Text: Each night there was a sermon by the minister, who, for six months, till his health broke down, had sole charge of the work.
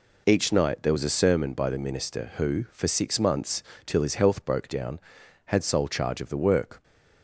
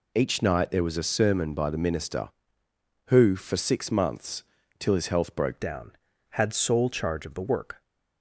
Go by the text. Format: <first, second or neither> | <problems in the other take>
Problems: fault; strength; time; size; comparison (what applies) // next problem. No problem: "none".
first | changes voice at "down"; from 5.5 s on; 2.3 s long